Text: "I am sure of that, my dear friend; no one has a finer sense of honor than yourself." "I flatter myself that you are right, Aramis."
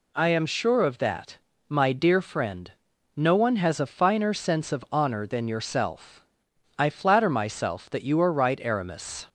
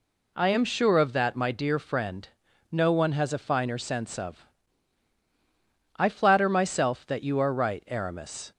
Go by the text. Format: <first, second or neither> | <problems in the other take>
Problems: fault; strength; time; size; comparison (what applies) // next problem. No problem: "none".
first | skips "honor than yourself"; at 5.2 s